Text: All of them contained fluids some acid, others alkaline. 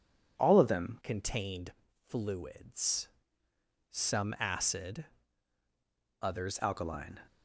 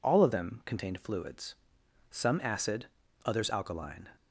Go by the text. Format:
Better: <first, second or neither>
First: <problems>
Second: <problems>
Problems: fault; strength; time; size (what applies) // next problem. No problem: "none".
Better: second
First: changes voice from "contained" to "others"; from 1.0 to 6.5 s; 5.5 s long // pauses between "contained" and "fluids"; slight; at 1.7 s; 0.34 s long // pauses between "fluids" and "some"; noticeable; at 3.0 s; 0.82 s long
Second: pauses between "fluids" and "some"; noticeable; at 1.5 s; 0.54 s long